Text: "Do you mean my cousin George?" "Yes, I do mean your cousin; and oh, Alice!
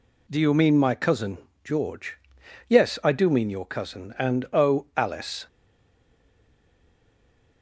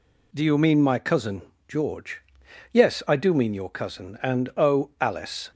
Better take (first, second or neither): second